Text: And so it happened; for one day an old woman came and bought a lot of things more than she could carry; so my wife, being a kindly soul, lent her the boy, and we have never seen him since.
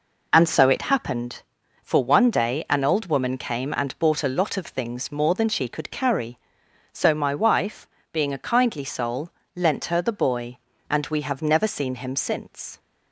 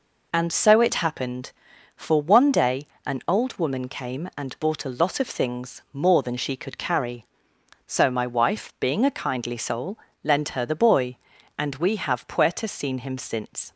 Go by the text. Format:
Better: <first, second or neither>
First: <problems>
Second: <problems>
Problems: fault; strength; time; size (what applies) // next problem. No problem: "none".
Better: first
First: none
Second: pauses between "day" and "an"; slight; at 2.8 s; 0.22 s long // says "puerta" for "never"; at 12.2 s